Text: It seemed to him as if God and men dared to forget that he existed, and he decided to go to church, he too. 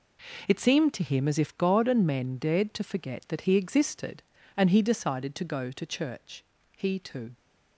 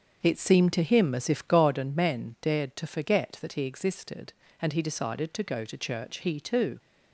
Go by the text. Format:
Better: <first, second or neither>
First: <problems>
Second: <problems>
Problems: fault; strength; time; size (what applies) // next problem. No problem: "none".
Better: first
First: none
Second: starts louder than the rest; until 1.8 s; 6.5 dB